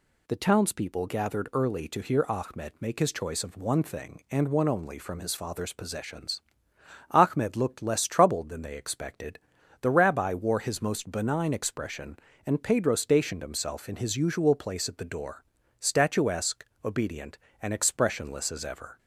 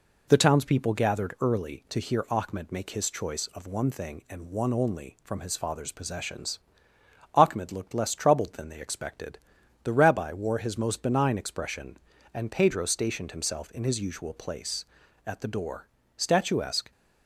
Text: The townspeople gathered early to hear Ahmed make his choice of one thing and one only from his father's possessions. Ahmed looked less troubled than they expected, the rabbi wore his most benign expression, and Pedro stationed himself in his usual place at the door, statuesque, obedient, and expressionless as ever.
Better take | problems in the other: first | stops before "obedient and expressionless as ever"; at 16.9 s

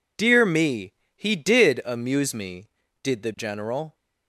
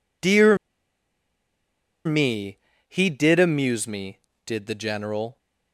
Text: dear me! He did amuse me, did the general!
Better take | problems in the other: first | pauses between "dear" and "me"; strong; at 0.5 s; 1.4 s long

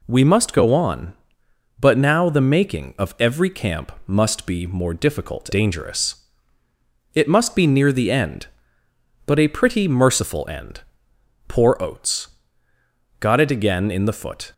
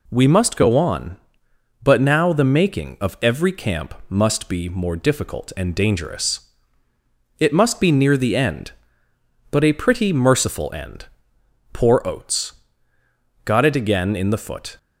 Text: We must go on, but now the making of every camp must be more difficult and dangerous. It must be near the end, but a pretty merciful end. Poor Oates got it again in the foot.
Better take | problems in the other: second | pauses between "camp" and "must"; slight; at 3.8 s; 0.16 s long; slight in the second // skips "and"; at 5.5 s // pauses between "Oates" and "got"; noticeable; at 12.2 s; 0.94 s long; noticeable in the second

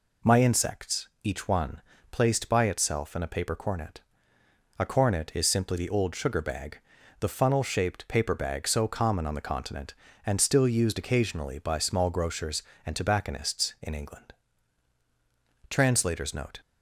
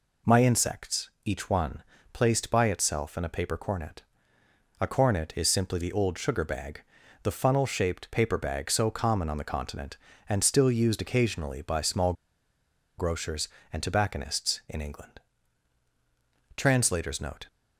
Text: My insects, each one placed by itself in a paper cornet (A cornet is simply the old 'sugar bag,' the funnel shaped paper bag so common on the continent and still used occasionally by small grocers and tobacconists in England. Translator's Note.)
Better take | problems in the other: first | pauses between "one" and "placed"; slight; at 1.8 s; 0.30 s long; slight in the first // pauses between "small" and "grocers"; noticeable; at 12.1 s; 0.84 s long

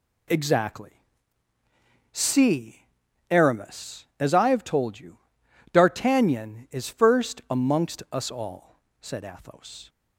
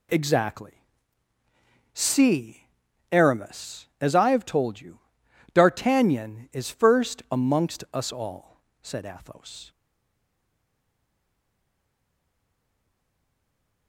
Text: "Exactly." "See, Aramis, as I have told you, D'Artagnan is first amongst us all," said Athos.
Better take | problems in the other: first | stays silent after the last word; strong; from 9.6 s on; 4.2 s long

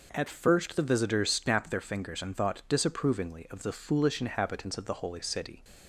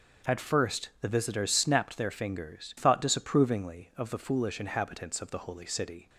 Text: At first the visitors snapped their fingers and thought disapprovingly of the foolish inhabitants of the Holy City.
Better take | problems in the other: first | starts louder than the rest; until 1.4 s; 6.5 dB // skips "and"; at 2.7 s

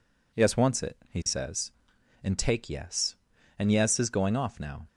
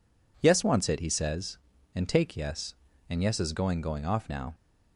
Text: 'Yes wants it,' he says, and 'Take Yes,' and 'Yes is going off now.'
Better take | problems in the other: first | says "going" twice; at 3.8 s

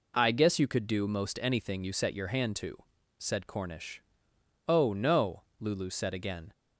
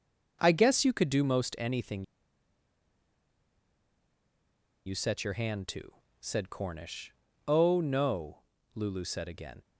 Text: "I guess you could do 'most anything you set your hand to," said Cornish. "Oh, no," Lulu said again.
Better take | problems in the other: first | pauses between "anything" and "you"; strong; at 2.0 s; 2.8 s long

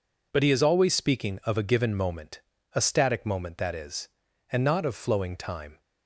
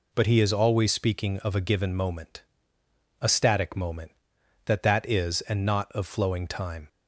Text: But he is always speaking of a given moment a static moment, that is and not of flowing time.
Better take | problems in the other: first | pauses between "moment" and "a"; noticeable; at 2.4 s; 0.80 s long; slight in the first // says "that" twice; at 4.8 s

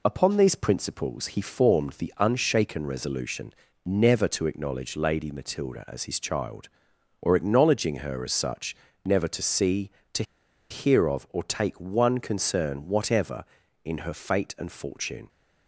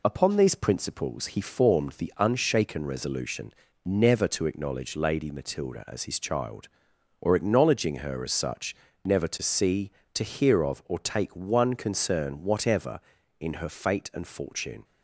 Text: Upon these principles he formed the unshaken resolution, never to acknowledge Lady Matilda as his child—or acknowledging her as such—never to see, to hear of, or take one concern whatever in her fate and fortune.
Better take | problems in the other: second | pauses between "to" and "hear"; noticeable; at 10.2 s; 0.47 s long

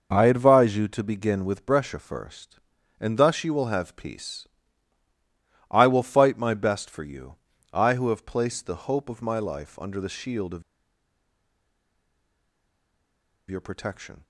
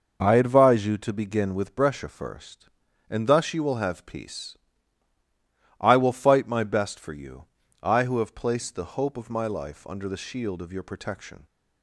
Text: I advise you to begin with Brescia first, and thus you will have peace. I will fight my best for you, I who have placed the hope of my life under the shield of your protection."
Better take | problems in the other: second | pauses between "of" and "your"; strong; at 10.6 s; 2.8 s long

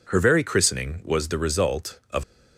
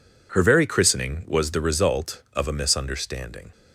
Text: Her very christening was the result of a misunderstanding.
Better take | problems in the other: second | stops before "a misunderstanding"; at 2.2 s

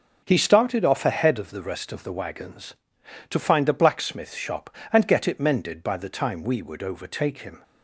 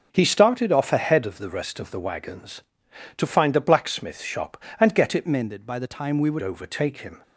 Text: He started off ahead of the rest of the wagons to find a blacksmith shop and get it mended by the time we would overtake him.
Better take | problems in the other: first | changes voice from "mended" to "would"; from 5.2 to 6.4 s; 1.2 s long

